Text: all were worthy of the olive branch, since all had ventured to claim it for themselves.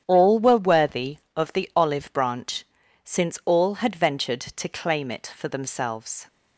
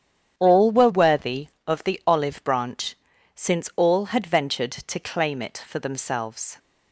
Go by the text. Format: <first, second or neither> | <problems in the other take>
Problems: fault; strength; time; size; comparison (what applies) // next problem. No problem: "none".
neither | starts louder than the rest; strong; the same in both